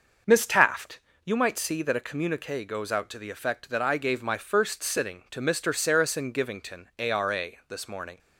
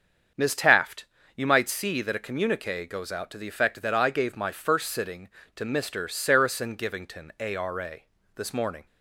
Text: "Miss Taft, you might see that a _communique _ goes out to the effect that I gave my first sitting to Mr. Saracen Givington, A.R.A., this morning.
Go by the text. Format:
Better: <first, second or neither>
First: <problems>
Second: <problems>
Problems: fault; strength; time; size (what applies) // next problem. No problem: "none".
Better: neither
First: starts louder than the rest; until 1.5 s; 6 dB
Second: starts louder than the rest; until 1.6 s; 7 dB